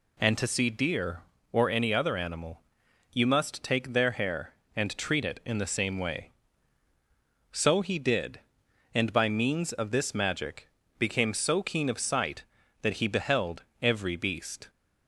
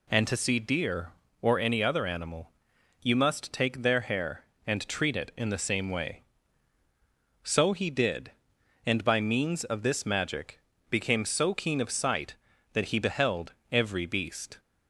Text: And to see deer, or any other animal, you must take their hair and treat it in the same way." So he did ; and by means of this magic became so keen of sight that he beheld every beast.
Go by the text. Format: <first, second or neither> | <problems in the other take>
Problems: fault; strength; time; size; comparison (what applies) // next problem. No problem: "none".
neither | pauses between "magic" and "became"; slight; the same in both // pauses between "beheld" and "every"; slight; the same in both